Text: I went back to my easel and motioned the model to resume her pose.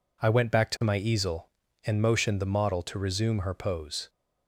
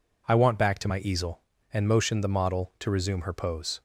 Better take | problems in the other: first | says "want" for "went"; at 0.3 s

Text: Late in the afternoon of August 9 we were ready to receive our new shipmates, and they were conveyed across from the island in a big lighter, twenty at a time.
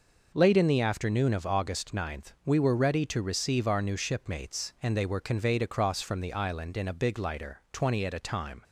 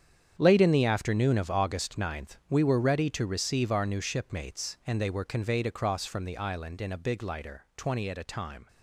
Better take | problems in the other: first | gets quieter; strong; throughout; 13 dB

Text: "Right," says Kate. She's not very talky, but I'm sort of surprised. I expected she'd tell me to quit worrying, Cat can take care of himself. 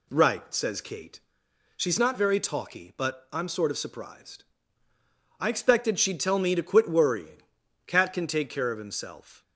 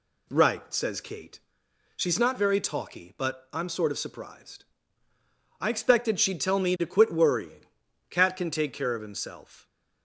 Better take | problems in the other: neither | none

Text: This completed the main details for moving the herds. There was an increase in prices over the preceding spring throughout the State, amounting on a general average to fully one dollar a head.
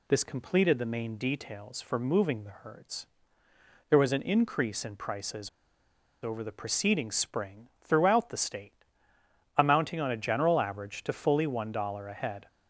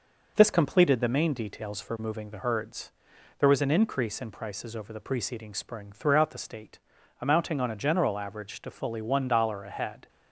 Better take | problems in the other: second | pauses between "prices" and "over"; noticeable; at 5.4 s; 0.73 s long

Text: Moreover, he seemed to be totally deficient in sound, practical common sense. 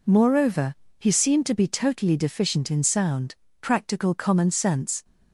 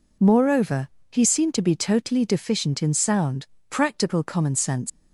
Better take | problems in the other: first | leaves "sense" unfinished; at 4.8 s; 110 ms

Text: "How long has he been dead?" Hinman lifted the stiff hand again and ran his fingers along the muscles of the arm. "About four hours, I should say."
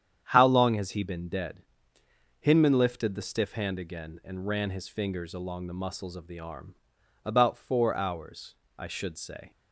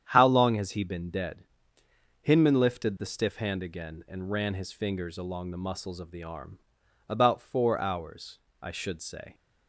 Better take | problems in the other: neither | starts louder than the rest; strong; the same in both

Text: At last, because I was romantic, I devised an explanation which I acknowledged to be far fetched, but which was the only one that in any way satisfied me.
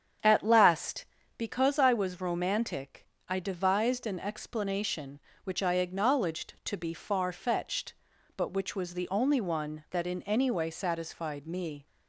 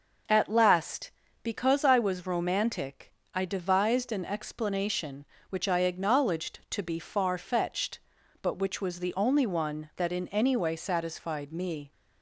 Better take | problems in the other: second | starts louder than the rest; strong; until 1.4 s; 8 dB

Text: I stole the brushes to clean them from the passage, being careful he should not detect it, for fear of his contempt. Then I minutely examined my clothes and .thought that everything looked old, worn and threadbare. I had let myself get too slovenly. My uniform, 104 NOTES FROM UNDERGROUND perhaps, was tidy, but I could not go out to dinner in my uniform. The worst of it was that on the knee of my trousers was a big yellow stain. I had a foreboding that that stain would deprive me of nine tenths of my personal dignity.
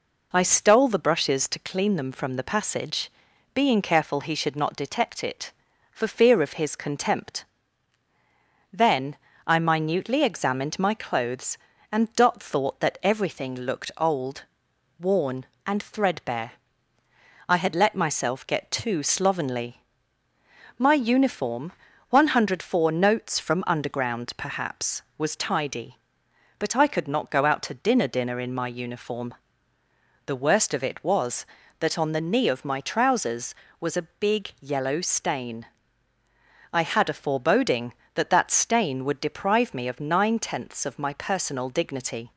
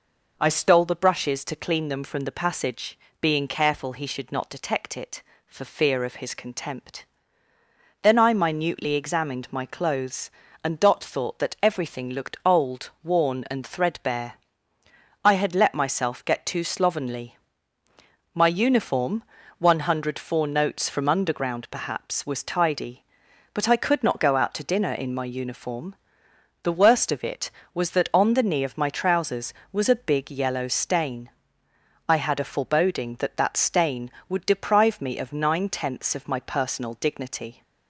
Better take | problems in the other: second | pauses between "Then" and "I"; slight; at 9.1 s; 0.28 s long // says "dinner" twice; at 28.0 s

